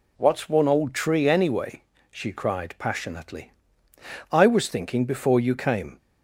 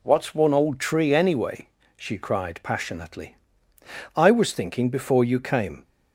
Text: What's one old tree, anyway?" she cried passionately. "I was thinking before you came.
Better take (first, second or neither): neither